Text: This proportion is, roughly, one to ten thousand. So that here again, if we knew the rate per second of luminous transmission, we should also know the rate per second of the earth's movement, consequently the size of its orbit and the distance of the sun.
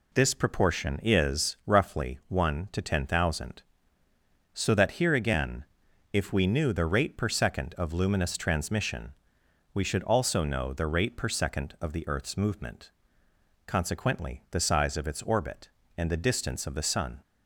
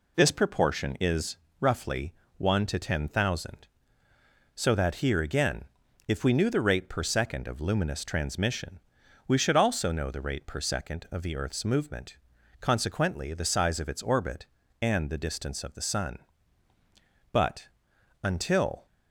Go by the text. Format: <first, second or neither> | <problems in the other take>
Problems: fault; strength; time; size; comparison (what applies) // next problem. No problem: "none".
first | goes on to say "But until"; from 17.3 s on; 1.5 s long